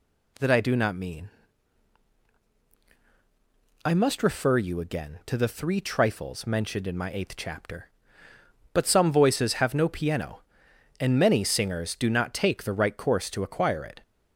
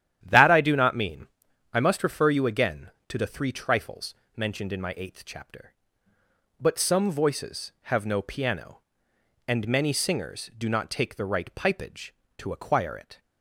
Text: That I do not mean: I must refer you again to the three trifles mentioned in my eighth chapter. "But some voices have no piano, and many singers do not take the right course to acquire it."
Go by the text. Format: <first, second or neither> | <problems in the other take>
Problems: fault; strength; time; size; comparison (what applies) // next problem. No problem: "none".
first | starts louder than the rest; strong; until 1.2 s; 11 dB // pauses between "trifles" and "mentioned"; slight; at 4.1 s; 0.22 s long // says "pipage" for "course"; at 11.5 s